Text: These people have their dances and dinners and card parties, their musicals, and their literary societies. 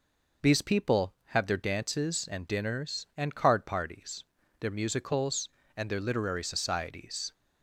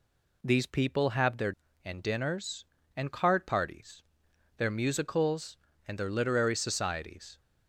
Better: first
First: none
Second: skips "dances"; at 1.6 s

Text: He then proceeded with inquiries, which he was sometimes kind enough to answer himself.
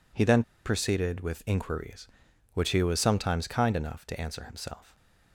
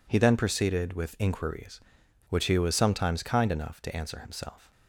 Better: second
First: pauses between "then" and "proceeded"; slight; at 0.4 s; 0.23 s long // stays silent after the last word; slight; from 4.8 s on; 0.5 s long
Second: none

